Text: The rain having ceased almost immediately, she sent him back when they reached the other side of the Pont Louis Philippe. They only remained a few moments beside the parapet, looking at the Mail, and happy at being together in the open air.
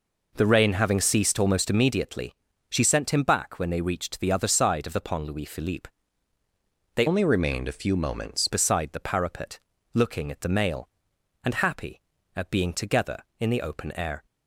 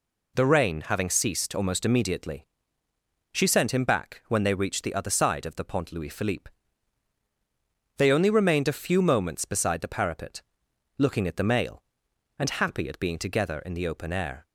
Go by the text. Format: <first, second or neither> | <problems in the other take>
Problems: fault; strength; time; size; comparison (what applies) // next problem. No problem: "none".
second | changes voice from "only" to "moments"; from 7.0 to 8.4 s; 1.4 s long